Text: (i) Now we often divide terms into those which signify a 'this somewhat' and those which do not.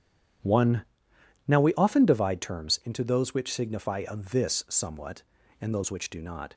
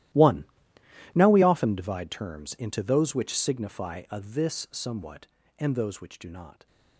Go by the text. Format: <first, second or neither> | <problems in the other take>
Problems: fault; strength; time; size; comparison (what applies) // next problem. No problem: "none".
first | gets quieter; strong; throughout; 18.5 dB